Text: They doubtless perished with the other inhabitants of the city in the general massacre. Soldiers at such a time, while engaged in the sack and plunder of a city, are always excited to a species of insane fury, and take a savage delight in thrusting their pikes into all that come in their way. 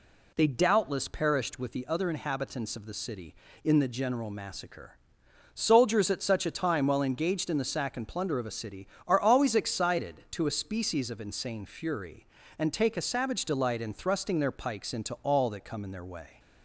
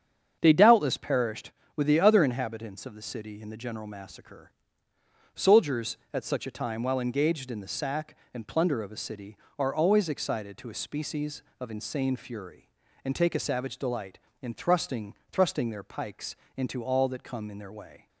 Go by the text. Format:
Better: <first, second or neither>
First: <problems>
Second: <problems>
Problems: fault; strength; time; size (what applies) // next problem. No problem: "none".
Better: first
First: none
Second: starts louder than the rest; strong; until 1.4 s; 7.5 dB // says "thrusting" twice; at 15.3 s // pauses between "pikes" and "into"; slight; at 16.3 s; 0.20 s long